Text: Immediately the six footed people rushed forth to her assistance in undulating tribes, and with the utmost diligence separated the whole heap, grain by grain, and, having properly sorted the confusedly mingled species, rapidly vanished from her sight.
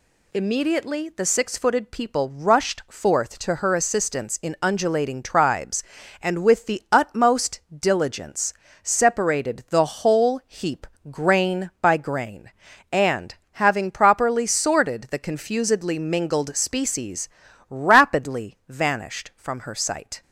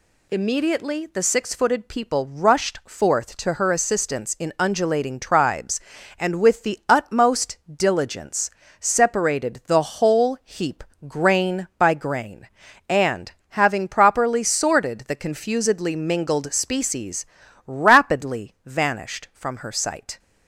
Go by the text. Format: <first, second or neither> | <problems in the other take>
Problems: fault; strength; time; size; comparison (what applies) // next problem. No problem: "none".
neither | pauses between "diligence" and "separated"; slight; the same in both